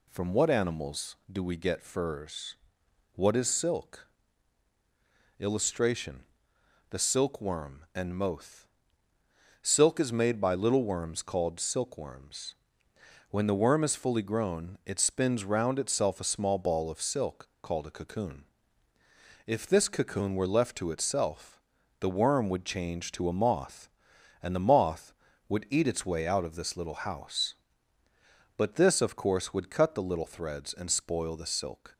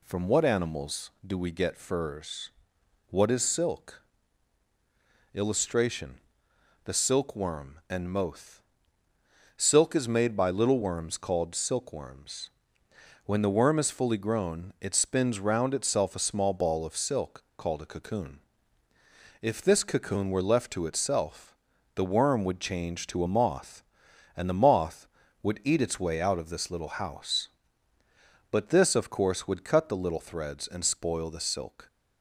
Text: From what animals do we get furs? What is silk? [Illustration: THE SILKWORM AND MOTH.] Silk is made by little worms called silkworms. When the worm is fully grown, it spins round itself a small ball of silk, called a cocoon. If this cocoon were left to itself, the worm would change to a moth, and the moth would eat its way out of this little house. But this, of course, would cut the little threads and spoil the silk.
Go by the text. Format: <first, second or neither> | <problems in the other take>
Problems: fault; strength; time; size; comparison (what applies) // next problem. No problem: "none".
neither | none